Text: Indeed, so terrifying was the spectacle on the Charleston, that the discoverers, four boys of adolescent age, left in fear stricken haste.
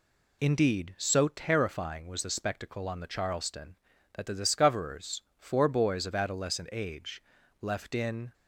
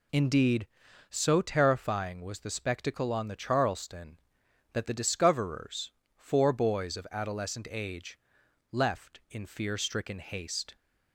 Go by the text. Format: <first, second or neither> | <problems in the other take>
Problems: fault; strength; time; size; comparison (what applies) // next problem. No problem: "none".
second | stops before "fear stricken haste"; at 8.3 s